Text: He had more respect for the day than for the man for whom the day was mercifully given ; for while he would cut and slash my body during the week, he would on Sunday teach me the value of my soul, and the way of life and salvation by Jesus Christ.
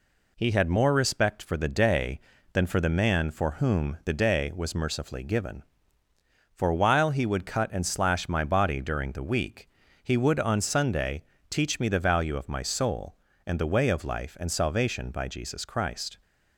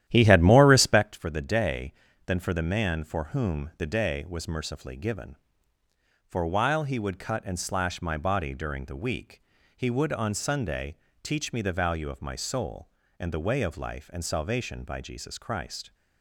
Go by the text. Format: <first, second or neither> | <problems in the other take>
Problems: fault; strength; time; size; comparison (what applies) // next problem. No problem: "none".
first | starts louder than the rest; strong; until 1.2 s; 12 dB // pauses between "Sunday" and "teach"; slight; at 10.9 s; 0.28 s long; slight in the first